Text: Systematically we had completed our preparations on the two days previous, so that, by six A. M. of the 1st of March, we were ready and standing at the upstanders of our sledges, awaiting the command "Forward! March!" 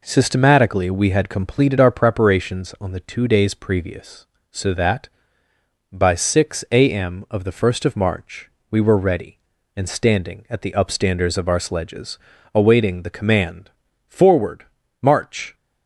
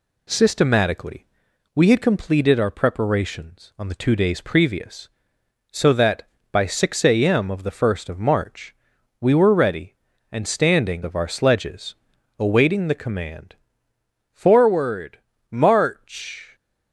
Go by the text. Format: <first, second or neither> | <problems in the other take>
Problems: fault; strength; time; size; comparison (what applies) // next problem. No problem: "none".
first | pauses between "Systematically" and "we"; noticeable; at 1.2 s; 0.50 s long // skips "at the upstanders"; at 11.0 s // pauses between "command" and "Forward"; noticeable; at 13.5 s; 0.76 s long; also in the first